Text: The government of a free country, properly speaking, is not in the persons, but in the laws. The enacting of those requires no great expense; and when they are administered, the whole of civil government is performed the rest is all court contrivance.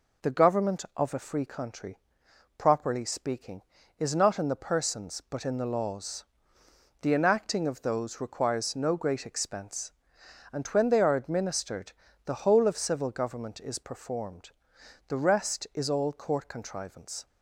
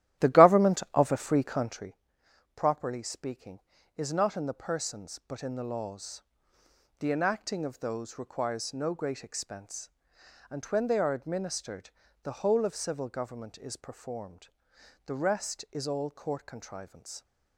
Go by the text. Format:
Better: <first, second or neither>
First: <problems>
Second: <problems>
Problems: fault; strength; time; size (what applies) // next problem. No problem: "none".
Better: first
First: pauses between "performed" and "the"; noticeable; at 14.5 s; 0.56 s long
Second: starts louder than the rest; strong; until 1.9 s; 14 dB // pauses between "performed" and "the"; noticeable; at 14.4 s; 0.56 s long